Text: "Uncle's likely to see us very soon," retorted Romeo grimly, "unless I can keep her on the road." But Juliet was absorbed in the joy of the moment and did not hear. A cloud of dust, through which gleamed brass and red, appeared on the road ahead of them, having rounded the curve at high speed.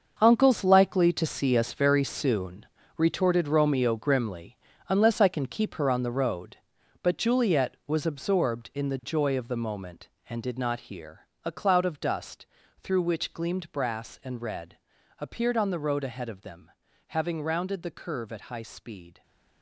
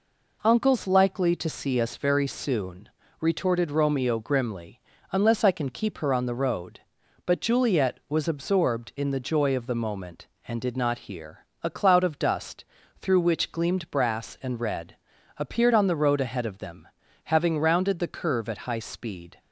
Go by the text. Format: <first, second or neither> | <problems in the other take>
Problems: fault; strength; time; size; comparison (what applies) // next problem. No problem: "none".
second | gets quieter; strong; throughout; 12 dB